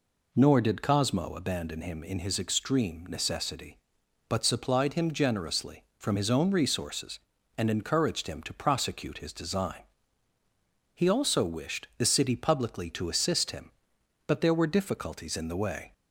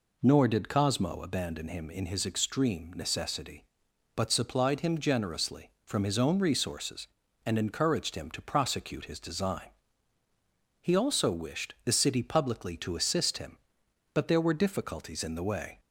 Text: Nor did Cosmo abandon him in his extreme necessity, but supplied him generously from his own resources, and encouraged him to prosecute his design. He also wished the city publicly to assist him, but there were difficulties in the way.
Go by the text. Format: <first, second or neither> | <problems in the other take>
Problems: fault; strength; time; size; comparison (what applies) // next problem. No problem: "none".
neither | none